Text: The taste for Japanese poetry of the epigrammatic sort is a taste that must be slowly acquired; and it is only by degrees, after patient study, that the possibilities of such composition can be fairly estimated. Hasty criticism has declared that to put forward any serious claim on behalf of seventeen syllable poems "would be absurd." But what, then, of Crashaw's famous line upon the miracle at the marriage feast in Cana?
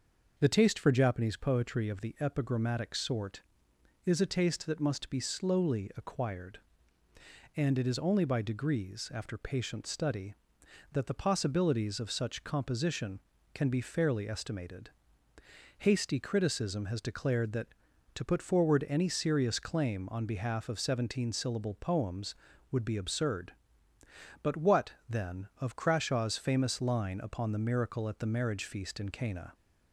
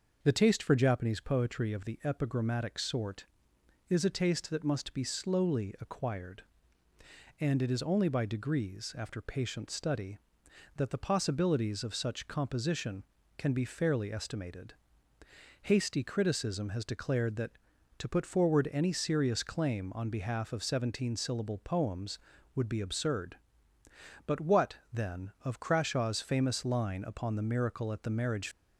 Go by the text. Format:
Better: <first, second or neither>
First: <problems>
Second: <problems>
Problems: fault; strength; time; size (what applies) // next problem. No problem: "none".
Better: first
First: none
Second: stops before "feast in Cana"; at 28.5 s